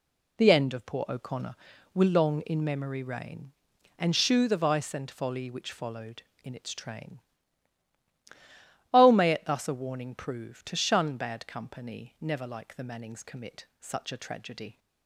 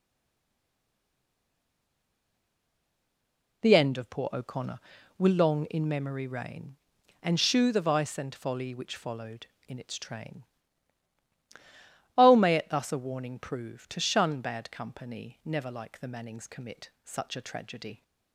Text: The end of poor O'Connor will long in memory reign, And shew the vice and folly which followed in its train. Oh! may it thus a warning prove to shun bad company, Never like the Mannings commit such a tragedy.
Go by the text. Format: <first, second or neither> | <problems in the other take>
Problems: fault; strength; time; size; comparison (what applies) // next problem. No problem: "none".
first | stays silent before the first word; strong; until 3.6 s; 3.6 s long